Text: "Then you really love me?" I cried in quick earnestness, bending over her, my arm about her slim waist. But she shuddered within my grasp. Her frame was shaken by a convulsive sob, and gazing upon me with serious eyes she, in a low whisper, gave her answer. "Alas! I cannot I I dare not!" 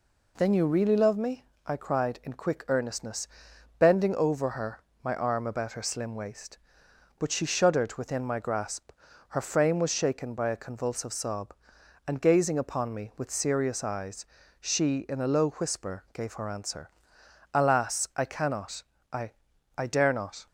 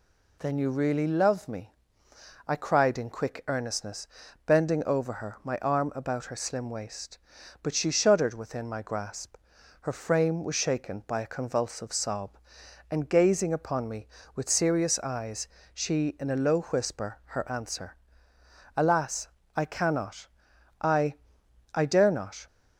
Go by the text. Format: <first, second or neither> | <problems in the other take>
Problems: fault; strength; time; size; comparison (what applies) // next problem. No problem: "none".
first | pauses between "eyes" and "she"; slight; at 15.4 s; 0.24 s long; slight in the first // skips "gave"; at 17.2 s // pauses between "cannot" and "I"; noticeable; at 20.2 s; 0.54 s long; slight in the first // pauses between "I" and "I"; noticeable; at 21.1 s; 0.60 s long; noticeable in the first